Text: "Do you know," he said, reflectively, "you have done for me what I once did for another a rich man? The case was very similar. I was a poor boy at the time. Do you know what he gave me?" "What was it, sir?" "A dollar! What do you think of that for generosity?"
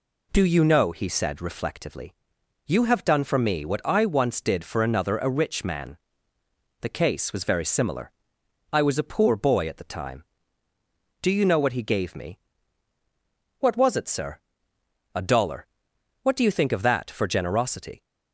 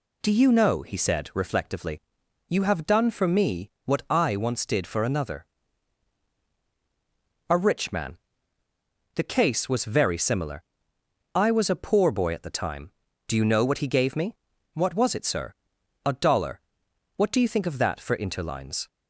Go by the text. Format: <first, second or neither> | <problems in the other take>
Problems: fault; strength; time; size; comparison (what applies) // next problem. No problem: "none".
first | pauses between "another" and "a"; strong; at 5.4 s; 2.0 s long // says "interlines" for "generosity"; at 18.1 s